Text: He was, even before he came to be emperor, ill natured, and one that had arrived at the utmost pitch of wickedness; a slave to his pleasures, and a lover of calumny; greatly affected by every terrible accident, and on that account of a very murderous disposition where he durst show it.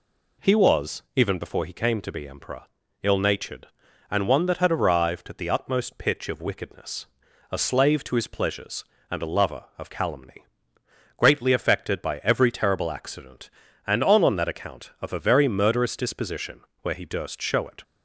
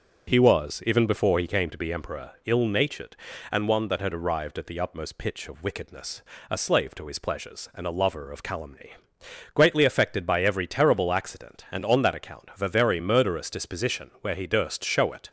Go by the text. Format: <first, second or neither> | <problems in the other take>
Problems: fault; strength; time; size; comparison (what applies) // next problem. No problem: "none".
second | says "on" twice; at 14.2 s // pauses between "disposition" and "where"; slight; at 16.6 s; 0.22 s long